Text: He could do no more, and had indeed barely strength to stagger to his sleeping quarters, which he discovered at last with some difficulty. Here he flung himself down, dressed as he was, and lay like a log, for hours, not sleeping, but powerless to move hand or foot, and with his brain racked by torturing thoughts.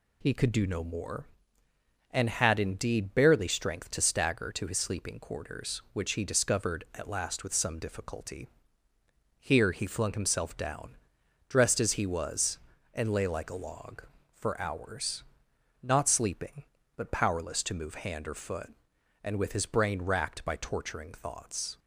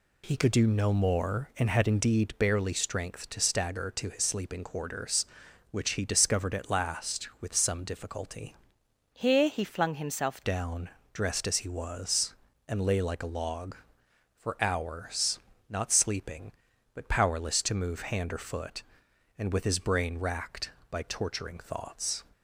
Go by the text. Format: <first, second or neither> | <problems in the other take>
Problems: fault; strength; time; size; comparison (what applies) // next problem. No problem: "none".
first | changes voice from "Here" to "himself"; from 9.1 to 10.4 s; 1.3 s long